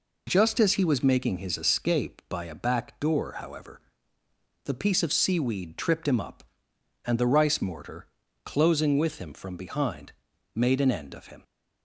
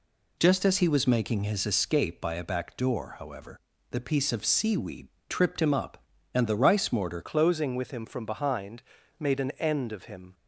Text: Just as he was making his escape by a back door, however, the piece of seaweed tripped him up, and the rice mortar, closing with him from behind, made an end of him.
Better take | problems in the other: first | pauses between "seaweed" and "tripped"; slight; at 5.0 s; 0.22 s long // changes voice at "closing"; from 7.2 s on; 3.1 s long

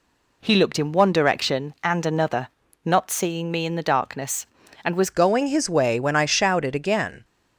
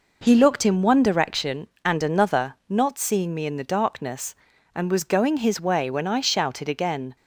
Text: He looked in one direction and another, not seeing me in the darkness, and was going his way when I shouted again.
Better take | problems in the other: second | changes voice at "going"; from 5.1 s on; 2.1 s long

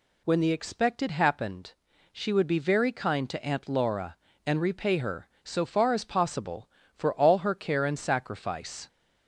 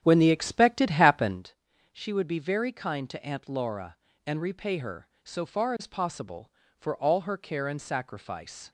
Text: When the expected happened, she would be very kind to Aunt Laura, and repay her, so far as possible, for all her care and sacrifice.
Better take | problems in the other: first | starts louder than the rest; strong; until 1.5 s; 9.5 dB

